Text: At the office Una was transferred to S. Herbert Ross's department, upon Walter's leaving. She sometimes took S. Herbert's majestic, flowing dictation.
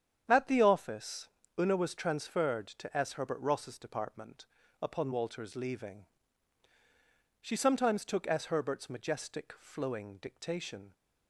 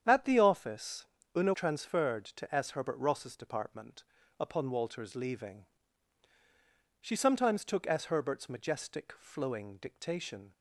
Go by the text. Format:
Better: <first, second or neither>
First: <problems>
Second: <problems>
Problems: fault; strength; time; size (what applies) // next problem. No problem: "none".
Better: first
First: starts louder than the rest; strong; until 1.2 s; 8.5 dB // pauses between "office" and "Una"; slight; at 1.2 s; 0.30 s long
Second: starts louder than the rest; strong; until 1.0 s; 8.5 dB // pauses between "office" and "Una"; slight; at 1.0 s; 0.30 s long // skips "was"; at 1.5 s